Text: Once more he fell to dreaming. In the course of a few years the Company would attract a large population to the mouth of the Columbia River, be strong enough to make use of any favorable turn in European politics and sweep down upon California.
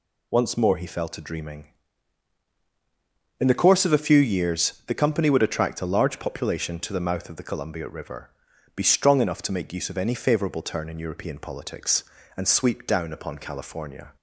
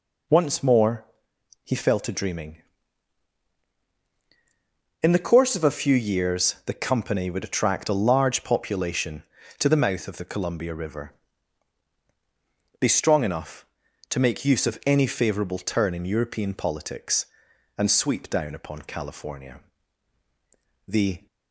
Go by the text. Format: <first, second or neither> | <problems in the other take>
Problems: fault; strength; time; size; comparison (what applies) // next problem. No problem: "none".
first | pauses between "more" and "he"; noticeable; at 1.0 s; 0.58 s long // goes on to say "The"; slight; from 20.8 s on; 0.38 s long